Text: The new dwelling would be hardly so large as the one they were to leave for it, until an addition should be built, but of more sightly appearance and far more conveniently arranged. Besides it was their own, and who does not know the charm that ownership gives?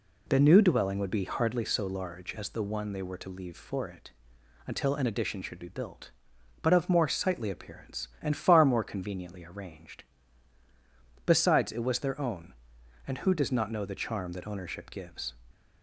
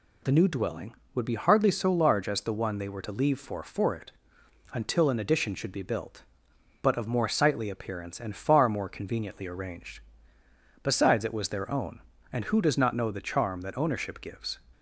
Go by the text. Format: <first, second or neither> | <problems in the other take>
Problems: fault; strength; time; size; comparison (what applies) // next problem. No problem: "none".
first | says "for" twice; at 3.6 s